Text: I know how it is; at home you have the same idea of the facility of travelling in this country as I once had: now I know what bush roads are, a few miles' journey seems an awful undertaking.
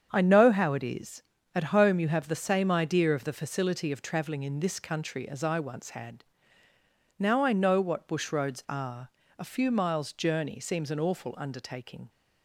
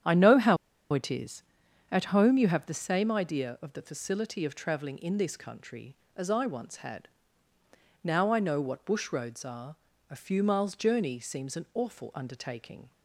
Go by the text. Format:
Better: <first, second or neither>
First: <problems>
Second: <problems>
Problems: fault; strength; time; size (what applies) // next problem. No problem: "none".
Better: first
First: starts louder than the rest; strong; until 1.1 s; 8 dB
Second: starts louder than the rest; strong; until 1.4 s; 9 dB // pauses between "how" and "it"; at 0.5 s; 0.36 s long